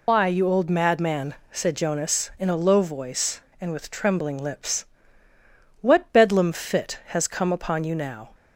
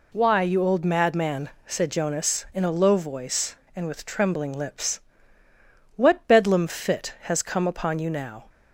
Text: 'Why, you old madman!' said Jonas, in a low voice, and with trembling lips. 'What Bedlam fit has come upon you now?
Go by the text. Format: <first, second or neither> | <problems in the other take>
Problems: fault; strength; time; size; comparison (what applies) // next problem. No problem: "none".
second | loses the start of "Why"; at 0.0 s; 90 ms